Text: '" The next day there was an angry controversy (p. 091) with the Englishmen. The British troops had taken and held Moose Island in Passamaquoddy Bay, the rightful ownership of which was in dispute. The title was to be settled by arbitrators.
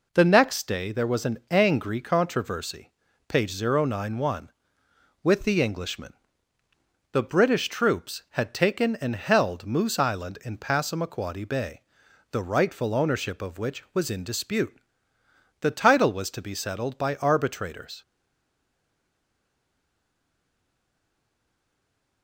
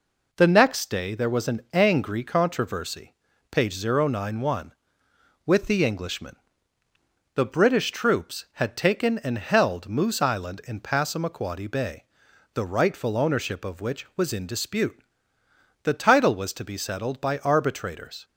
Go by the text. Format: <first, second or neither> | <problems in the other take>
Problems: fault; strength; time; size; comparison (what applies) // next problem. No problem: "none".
second | stays silent after the last word; strong; from 18.0 s on; 4.2 s long